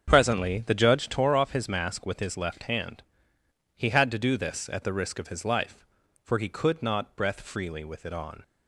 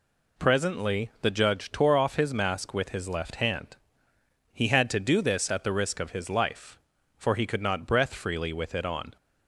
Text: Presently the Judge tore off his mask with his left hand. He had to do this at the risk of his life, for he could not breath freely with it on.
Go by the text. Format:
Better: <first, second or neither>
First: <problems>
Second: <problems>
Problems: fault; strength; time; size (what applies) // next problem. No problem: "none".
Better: second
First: starts louder than the rest; until 1.2 s; 7 dB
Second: none